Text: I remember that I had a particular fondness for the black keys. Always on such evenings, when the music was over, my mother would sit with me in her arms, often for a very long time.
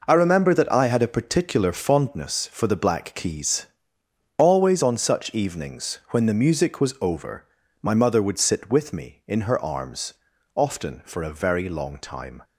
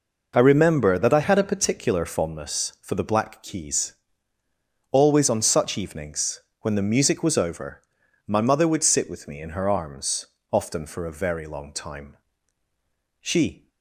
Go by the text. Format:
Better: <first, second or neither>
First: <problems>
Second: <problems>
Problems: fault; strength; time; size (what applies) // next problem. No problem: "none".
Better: first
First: none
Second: goes on to say "She"; slight; from 13.2 s on; 0.48 s long